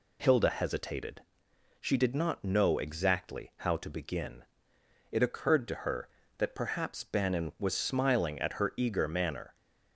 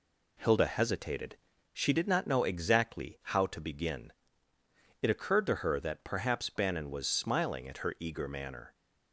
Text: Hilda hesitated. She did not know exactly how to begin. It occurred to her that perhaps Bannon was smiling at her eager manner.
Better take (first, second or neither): neither